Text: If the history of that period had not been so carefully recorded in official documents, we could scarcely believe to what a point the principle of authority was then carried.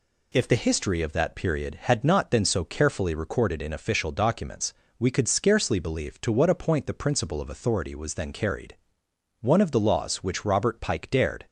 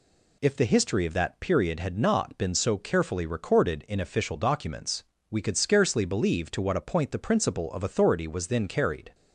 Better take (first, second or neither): second